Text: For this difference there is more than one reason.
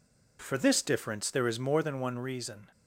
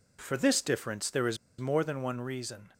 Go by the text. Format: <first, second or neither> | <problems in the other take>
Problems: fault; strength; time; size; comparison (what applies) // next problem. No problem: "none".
first | pauses between "is" and "more"; slight; at 1.3 s; 0.23 s long